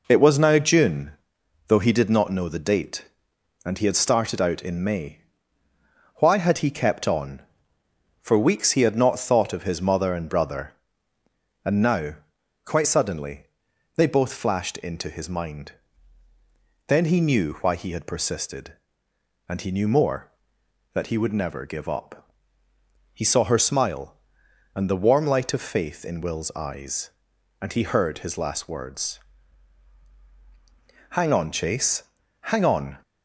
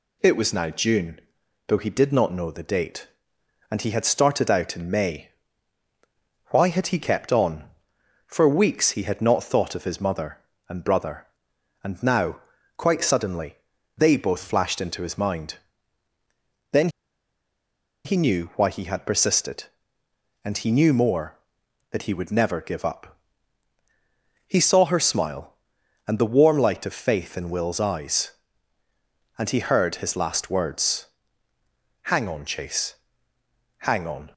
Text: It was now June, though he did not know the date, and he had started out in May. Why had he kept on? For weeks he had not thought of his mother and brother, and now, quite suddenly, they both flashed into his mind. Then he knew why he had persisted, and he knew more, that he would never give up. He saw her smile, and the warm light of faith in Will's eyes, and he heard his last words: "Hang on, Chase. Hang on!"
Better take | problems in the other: first | pauses between "Then" and "he"; at 16.8 s; 1.1 s long

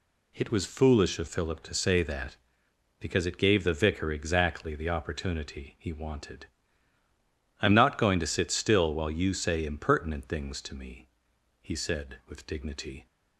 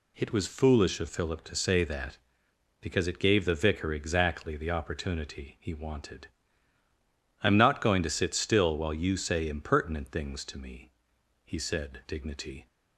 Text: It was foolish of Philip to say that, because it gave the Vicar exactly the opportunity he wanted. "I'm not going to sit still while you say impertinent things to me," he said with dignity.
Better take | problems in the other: first | skips "with"; at 12.0 s

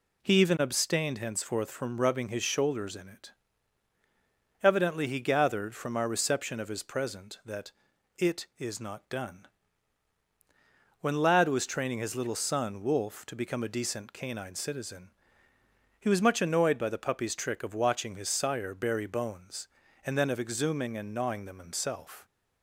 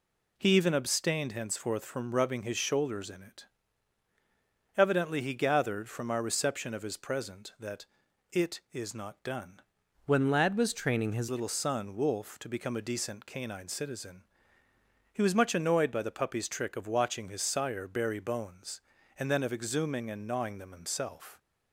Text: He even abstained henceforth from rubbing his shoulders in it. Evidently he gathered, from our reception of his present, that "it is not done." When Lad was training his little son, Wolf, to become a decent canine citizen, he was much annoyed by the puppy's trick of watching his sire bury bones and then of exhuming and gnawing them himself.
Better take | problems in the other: first | pauses between "that" and "it"; at 7.8 s; 0.44 s long; also in the first // changes voice from "When" to "his"; from 10.0 to 11.2 s; 1.2 s long

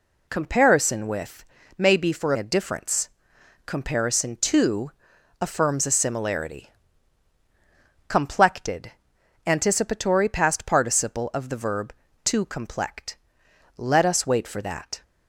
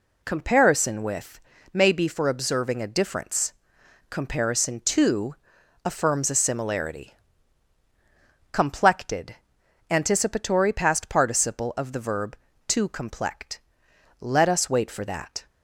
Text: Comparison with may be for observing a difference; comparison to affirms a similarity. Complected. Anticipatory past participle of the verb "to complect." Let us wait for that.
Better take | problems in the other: second | pauses between "with" and "may"; slight; at 1.4 s; 0.32 s long; slight in the second // skips "observing"; at 2.3 s // pauses between "to" and "affirms"; noticeable; at 4.9 s; 0.50 s long; noticeable in the second

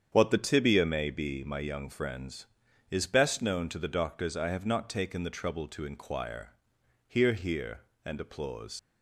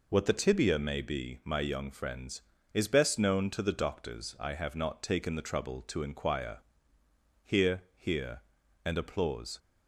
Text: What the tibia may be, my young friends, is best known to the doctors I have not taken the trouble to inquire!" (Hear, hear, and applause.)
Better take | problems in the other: second | starts louder than the rest; strong; until 1.1 s; 8 dB // leaves "applause" unfinished; at 8.7 s; 55 ms

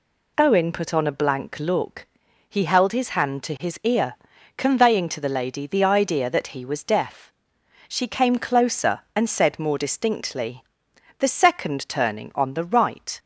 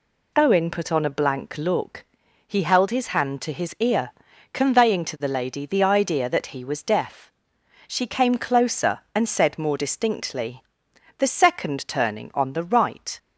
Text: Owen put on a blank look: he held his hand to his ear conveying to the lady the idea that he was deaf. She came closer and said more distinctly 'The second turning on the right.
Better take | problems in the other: neither | pauses between "ear" and "conveying"; the same in both // pauses between "distinctly" and "The"; noticeable; the same in both

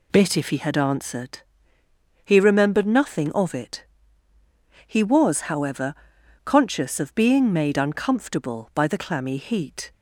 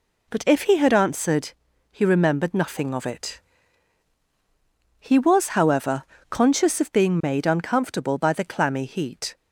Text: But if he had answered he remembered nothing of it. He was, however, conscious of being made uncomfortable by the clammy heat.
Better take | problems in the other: second | says "Bit" for "But"; at 0.1 s // pauses between "answered" and "he"; noticeable; at 1.3 s; 0.84 s long; also in the second

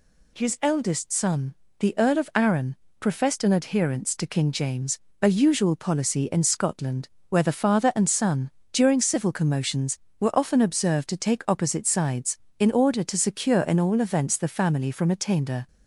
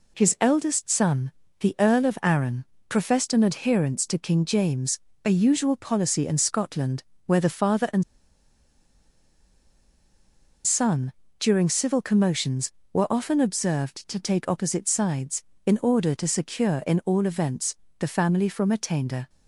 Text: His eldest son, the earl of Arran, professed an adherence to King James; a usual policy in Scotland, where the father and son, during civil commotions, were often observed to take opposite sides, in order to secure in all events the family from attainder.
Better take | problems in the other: first | pauses between "and" and "son"; strong; at 8.0 s; 2.6 s long // pauses between "events" and "the"; slight; at 17.7 s; 0.22 s long

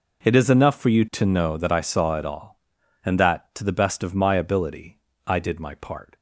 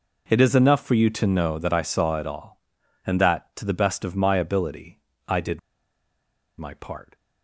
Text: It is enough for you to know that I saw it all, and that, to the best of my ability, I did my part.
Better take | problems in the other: first | pauses between "did" and "my"; at 5.5 s; 0.99 s long

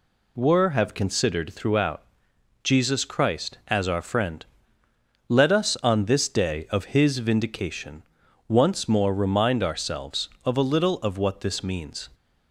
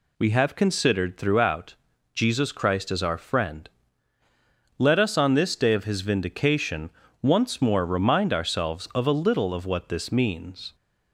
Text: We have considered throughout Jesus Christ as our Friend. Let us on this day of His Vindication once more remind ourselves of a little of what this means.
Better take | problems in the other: second | says "Were" for "We"; at 0.3 s // pauses between "throughout" and "Jesus"; noticeable; at 2.0 s; 0.60 s long; also in the second // pauses between "Vindication" and "once"; at 8.0 s; 0.44 s long; slight in the second

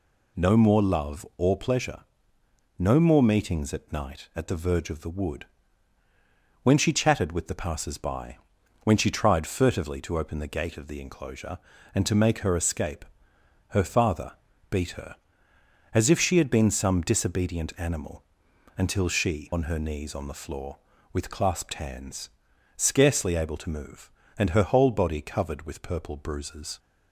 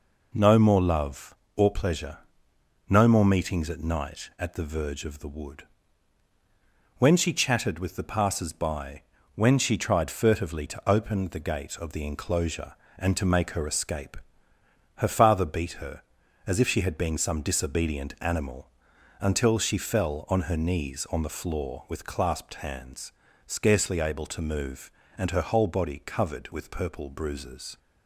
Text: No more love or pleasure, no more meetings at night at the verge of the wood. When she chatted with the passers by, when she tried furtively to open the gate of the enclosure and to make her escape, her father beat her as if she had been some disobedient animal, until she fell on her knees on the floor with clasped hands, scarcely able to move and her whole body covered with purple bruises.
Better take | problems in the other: second | pauses between "father" and "beat"; at 14.3 s; 0.38 s long // skips "fell"; at 19.5 s

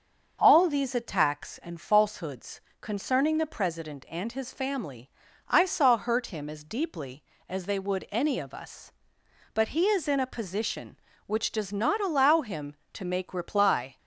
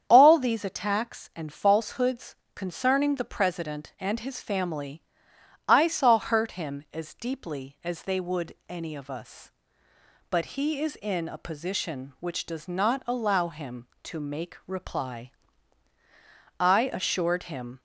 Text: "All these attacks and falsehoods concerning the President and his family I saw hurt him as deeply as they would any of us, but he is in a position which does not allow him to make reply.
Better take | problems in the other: first | starts louder than the rest; strong; until 1.0 s; 8.5 dB; also in the first // pauses between "falsehoods" and "concerning"; slight; at 2.3 s; 0.18 s long; slight in the first // pauses between "family" and "I"; noticeable; at 5.0 s; 0.64 s long; also in the first // goes on to say "I assured him"; noticeable; from 16.6 s on; 1.2 s long

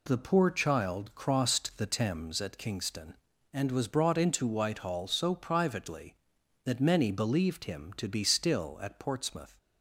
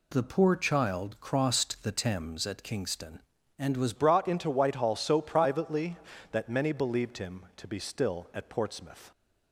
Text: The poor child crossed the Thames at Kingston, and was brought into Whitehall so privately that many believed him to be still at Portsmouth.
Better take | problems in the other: first | changes voice at "brought"; from 3.9 s on; 5.2 s long

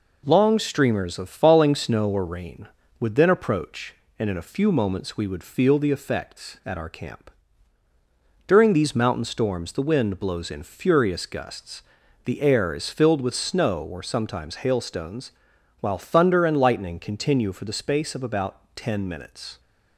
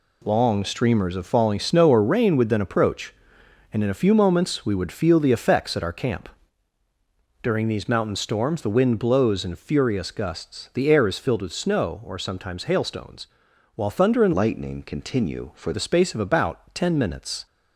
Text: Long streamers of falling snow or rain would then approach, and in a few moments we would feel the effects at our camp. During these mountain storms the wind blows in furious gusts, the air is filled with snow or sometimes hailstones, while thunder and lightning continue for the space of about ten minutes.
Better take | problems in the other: first | changes voice from "lightning" to "for"; from 14.3 to 15.7 s; 1.4 s long

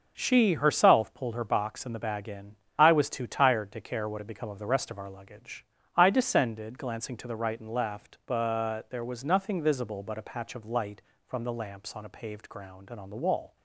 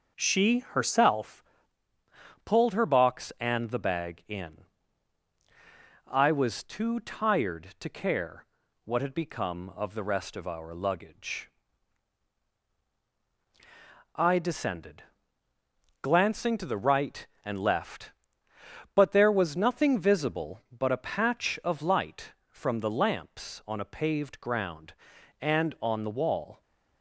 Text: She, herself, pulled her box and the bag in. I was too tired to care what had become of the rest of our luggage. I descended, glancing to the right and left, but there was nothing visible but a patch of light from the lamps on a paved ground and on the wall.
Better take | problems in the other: first | changes voice at "pulled"; from 2.4 s on; 24.2 s long // pauses between "care" and "what"; at 8.4 s; 0.38 s long

